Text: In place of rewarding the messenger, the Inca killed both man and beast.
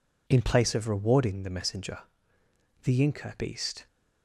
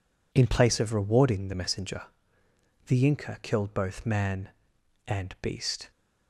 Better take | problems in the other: second | skips "killed both man and"; at 3.3 s

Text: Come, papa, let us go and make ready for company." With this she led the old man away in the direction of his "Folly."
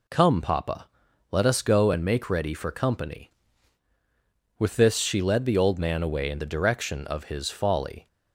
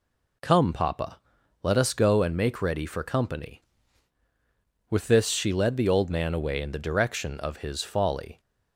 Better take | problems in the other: neither | none

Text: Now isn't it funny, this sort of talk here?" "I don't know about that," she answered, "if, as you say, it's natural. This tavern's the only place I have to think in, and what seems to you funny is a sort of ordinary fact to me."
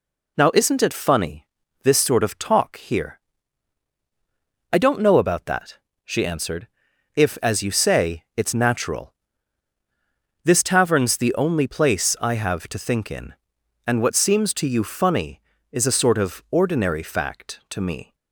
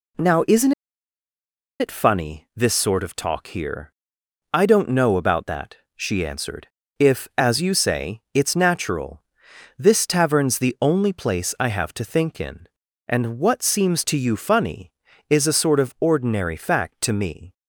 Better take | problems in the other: first | pauses between "isn't" and "it"; at 0.7 s; 1.0 s long

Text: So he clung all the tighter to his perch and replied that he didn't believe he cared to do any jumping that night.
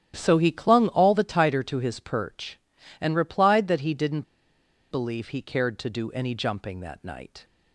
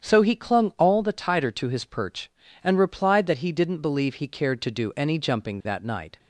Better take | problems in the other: second | starts louder than the rest; strong; until 1.1 s; 11 dB; strong in the second // pauses between "didn't" and "believe"; noticeable; at 4.2 s; 0.66 s long

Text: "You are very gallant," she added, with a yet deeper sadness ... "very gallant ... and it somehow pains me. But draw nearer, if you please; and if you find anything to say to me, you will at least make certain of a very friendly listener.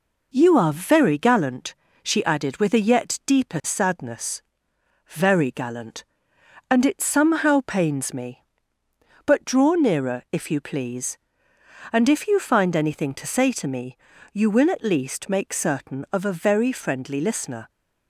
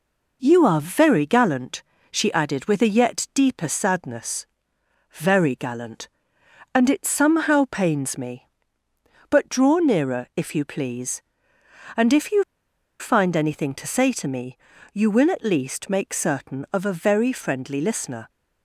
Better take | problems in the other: first | pauses between "you" and "find"; noticeable; at 12.4 s; 0.57 s long

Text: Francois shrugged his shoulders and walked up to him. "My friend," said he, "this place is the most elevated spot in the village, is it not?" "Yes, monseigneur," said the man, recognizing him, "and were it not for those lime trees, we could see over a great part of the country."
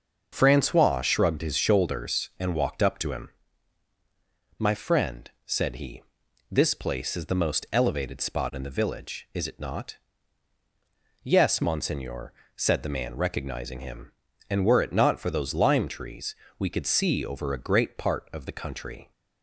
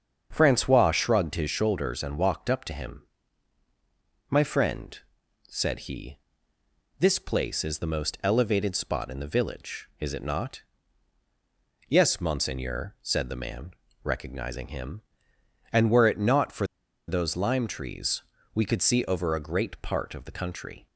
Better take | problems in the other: first | starts louder than the rest; until 1.3 s; 6.5 dB; noticeable in the first // pauses between "for" and "those"; at 16.6 s; 0.42 s long

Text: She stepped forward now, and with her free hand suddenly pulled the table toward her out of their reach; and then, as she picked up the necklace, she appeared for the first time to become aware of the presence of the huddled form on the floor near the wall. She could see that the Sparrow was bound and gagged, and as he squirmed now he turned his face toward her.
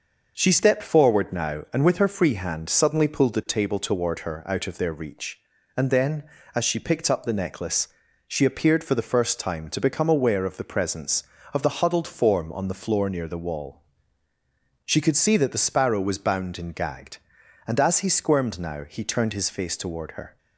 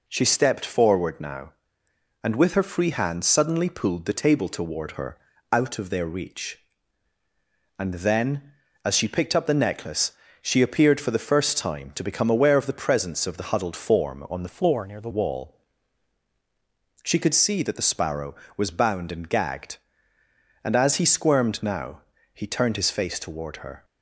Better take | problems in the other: first | pauses between "her" and "out"; slight; at 5.1 s; 0.34 s long // changes voice from "floor" to "the"; from 14.4 to 15.0 s; 0.6 s long // pauses between "now" and "he"; slight; at 22.0 s; 0.32 s long

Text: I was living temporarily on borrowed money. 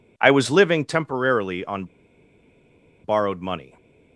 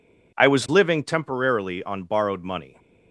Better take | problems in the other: second | pauses between "on" and "borrowed"; at 1.8 s; 1.2 s long

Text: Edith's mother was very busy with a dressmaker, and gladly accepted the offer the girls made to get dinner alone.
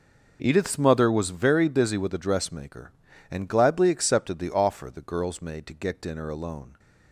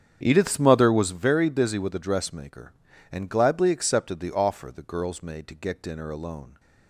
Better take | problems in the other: first | starts louder than the rest; strong; until 1.2 s; 8 dB

